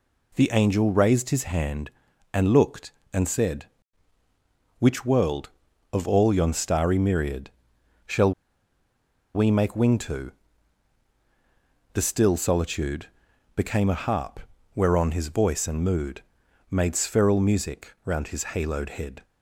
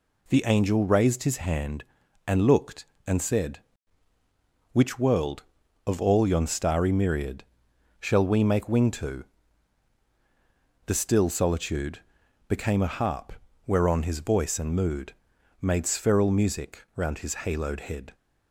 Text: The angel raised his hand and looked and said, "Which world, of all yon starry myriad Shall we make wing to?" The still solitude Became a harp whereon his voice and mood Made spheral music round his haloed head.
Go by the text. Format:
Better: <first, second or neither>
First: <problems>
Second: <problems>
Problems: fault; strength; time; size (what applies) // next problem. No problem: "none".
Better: second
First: pauses between "myriad" and "Shall"; noticeable; at 7.5 s; 0.56 s long // pauses between "Shall" and "we"; at 8.3 s; 1.0 s long // pauses between "solitude" and "Became"; noticeable; at 13.0 s; 0.48 s long // pauses between "harp" and "whereon"; at 14.3 s; 0.38 s long // pauses between "mood" and "Made"; noticeable; at 16.2 s; 0.48 s long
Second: pauses between "myriad" and "Shall"; noticeable; at 7.4 s; 0.56 s long // pauses between "solitude" and "Became"; noticeable; at 12.0 s; 0.48 s long // pauses between "harp" and "whereon"; at 13.3 s; 0.36 s long // pauses between "mood" and "Made"; noticeable; at 15.1 s; 0.47 s long